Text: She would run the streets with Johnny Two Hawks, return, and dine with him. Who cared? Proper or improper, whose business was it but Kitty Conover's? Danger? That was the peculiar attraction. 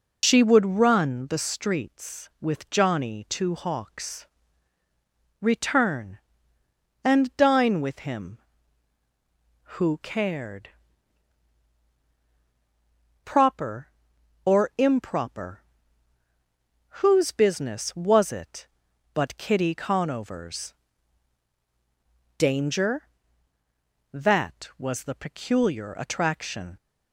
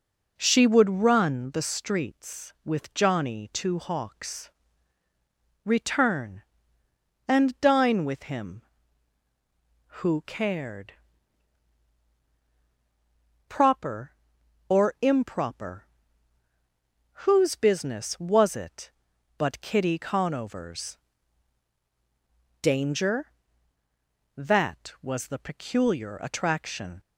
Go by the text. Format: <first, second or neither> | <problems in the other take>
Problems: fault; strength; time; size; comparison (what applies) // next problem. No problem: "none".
second | loses the start of "She"; at 0.2 s; 90 ms